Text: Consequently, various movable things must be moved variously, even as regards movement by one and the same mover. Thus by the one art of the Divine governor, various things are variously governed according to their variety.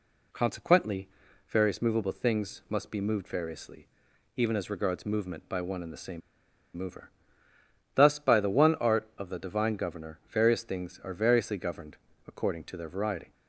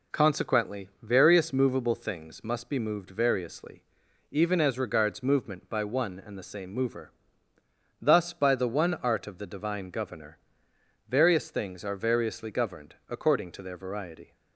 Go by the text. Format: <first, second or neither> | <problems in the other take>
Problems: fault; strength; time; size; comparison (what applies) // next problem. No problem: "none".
second | pauses between "same" and "mover"; noticeable; at 6.2 s; 0.56 s long // pauses between "governed" and "according"; slight; at 11.9 s; 0.30 s long